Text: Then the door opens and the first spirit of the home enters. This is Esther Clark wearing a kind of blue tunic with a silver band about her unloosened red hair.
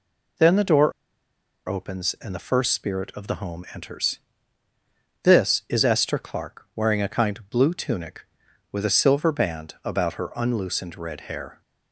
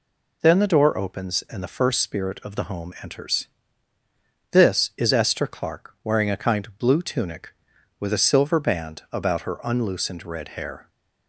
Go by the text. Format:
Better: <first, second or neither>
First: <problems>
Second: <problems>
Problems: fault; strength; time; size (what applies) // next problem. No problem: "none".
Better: second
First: pauses between "door" and "opens"; noticeable; at 0.9 s; 0.76 s long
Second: none